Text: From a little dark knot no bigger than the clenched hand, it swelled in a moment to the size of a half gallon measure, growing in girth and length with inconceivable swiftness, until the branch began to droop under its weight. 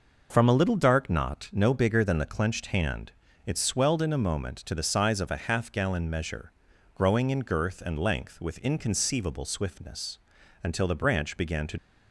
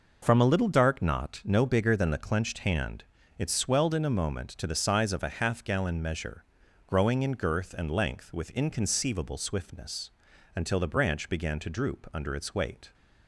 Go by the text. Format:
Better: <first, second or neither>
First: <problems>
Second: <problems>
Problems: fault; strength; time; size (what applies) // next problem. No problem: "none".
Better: second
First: stops before "droop under its weight"; at 11.7 s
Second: none